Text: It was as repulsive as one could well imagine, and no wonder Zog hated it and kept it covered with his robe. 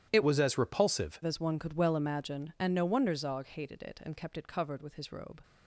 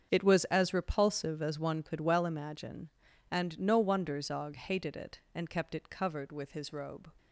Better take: second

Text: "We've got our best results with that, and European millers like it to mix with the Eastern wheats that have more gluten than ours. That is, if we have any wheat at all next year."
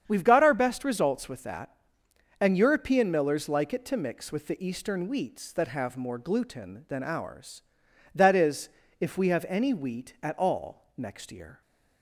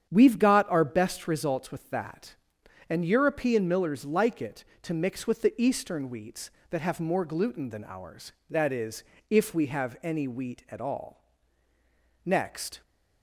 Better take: first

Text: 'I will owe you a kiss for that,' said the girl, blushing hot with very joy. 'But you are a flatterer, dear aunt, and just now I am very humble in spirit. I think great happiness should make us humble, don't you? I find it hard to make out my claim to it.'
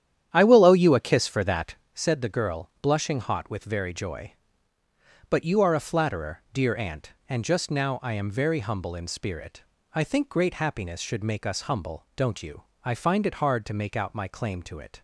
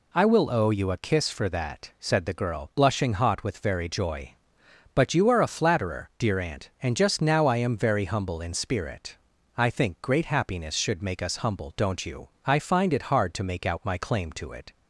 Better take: second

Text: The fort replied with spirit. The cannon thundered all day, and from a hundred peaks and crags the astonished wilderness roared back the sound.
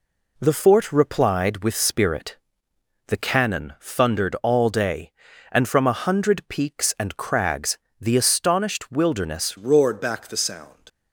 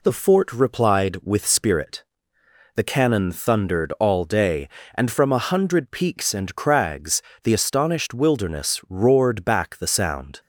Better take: second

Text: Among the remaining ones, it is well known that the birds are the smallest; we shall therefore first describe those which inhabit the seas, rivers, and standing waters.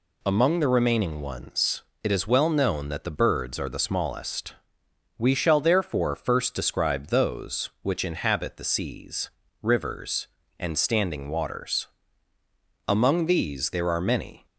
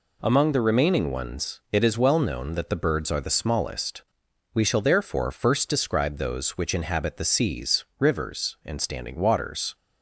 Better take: second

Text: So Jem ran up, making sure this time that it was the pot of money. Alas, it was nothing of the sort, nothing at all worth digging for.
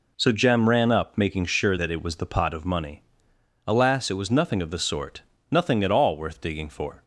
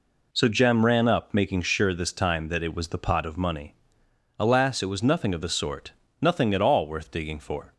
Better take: second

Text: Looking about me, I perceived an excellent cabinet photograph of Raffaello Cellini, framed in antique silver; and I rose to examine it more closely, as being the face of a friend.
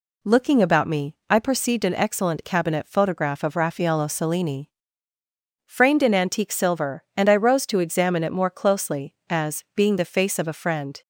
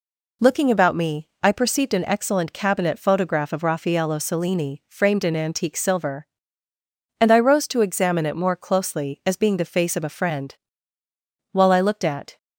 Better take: first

